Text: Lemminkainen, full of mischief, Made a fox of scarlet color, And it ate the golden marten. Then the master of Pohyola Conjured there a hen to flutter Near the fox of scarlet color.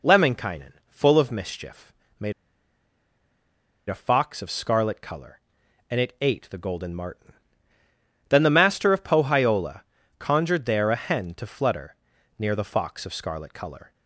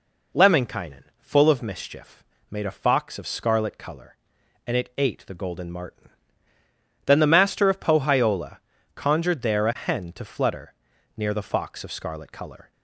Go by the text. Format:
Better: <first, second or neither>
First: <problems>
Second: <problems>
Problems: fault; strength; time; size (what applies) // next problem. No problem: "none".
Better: second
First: pauses between "Made" and "a"; strong; at 2.3 s; 1.5 s long // pauses between "Pohyola" and "Conjured"; slight; at 9.8 s; 0.36 s long // pauses between "flutter" and "Near"; at 11.9 s; 0.44 s long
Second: pauses between "Pohyola" and "Conjured"; slight; at 8.5 s; 0.36 s long // pauses between "flutter" and "Near"; at 10.7 s; 0.44 s long